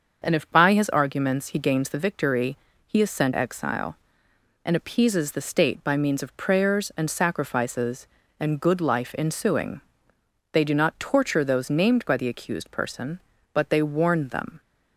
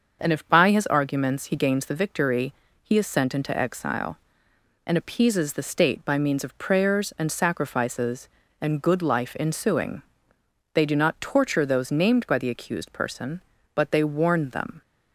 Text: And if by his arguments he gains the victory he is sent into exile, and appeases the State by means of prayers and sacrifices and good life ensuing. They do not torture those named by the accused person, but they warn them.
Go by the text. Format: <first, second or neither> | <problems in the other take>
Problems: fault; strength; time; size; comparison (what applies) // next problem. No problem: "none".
second | starts louder than the rest; until 1.2 s; 6.5 dB; also in the second // pauses between "victory" and "he"; slight; at 2.5 s; 0.30 s long; slight in the second // skips "into"; at 3.3 s